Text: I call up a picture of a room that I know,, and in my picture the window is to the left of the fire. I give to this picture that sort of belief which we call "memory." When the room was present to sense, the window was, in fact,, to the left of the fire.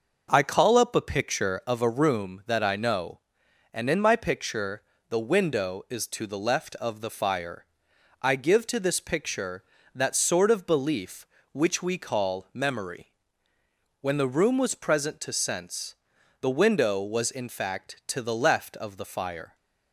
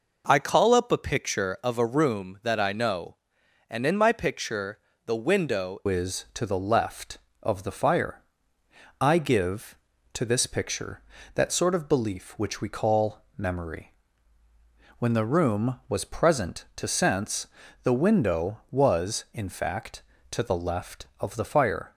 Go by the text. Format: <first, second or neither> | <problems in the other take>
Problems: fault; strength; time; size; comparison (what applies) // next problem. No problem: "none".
first | pauses between "picture" and "the"; slight; at 4.7 s; 0.26 s long; slight in the first // changes voice at "is"; from 5.8 s on; 16.1 s long // pauses between "call" and "memory"; slight; at 13.2 s; 0.16 s long